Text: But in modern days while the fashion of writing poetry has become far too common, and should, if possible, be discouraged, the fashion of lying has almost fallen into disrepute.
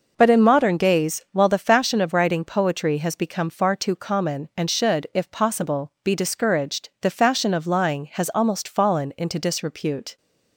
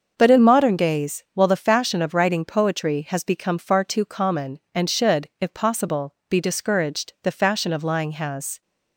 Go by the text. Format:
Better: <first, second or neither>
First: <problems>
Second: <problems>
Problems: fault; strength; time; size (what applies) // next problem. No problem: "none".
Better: first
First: none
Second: starts louder than the rest; until 1.1 s; 6.5 dB // stops before "almost fallen into disrepute"; at 8.6 s